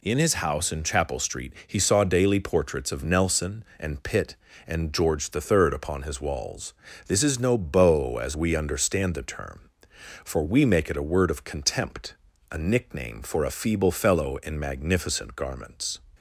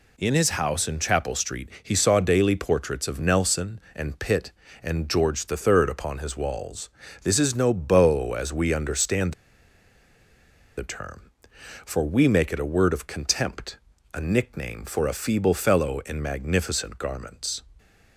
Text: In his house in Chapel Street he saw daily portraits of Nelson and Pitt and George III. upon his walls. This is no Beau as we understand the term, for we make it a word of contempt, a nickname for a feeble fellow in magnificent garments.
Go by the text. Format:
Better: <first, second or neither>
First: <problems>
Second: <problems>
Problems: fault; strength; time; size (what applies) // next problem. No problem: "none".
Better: first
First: none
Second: pauses between "understand" and "the"; strong; at 9.3 s; 1.4 s long